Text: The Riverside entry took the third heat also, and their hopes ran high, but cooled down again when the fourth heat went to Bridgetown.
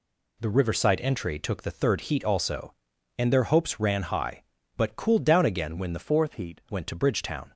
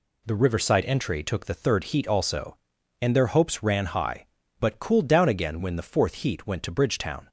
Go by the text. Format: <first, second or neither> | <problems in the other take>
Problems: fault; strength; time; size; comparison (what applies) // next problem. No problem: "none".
second | changes voice from "fourth" to "heat"; from 6.0 to 6.6 s; 0.6 s long